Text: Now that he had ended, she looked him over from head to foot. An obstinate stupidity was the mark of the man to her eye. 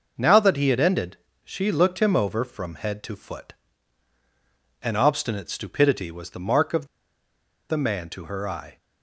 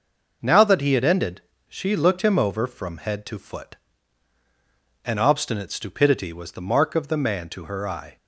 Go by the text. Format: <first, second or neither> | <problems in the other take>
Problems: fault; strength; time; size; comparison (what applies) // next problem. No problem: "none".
second | pauses between "of" and "the"; noticeable; at 6.8 s; 0.84 s long